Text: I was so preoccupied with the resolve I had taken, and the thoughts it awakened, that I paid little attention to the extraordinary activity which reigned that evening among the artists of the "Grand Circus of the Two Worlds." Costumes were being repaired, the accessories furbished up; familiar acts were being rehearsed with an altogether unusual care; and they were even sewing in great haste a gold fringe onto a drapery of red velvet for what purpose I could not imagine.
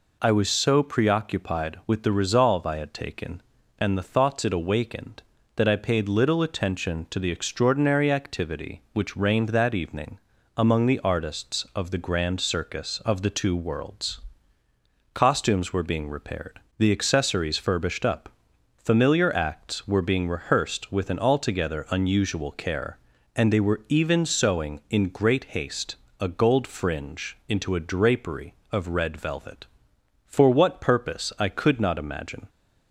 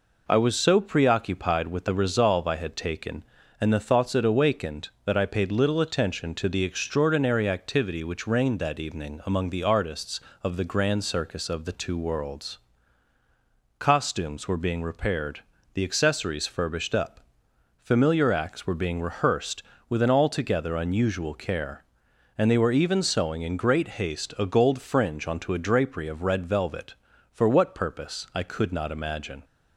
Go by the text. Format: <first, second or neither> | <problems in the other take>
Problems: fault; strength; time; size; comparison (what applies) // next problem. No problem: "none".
second | pauses between "evening" and "among"; at 10.1 s; 0.38 s long // pauses between "haste" and "a"; slight; at 25.9 s; 0.24 s long // says "into" for "onto"; at 27.4 s